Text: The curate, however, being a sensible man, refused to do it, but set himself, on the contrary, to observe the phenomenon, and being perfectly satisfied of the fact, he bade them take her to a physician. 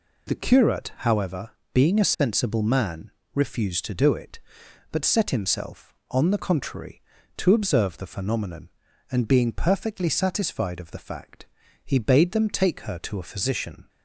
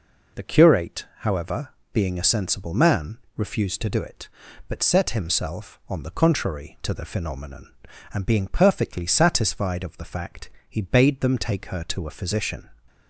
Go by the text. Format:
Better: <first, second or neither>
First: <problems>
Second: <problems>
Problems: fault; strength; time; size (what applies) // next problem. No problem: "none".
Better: first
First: none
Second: skips "observe"; at 6.9 s